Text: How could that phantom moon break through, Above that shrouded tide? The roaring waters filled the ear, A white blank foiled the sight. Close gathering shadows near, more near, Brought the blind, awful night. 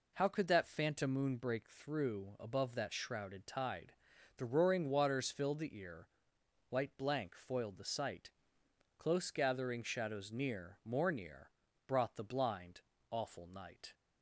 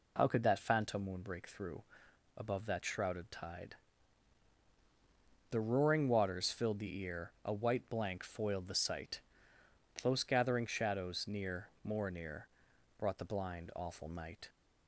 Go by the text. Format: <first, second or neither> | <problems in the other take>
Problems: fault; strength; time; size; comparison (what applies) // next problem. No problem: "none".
second | skips "A"; at 6.3 s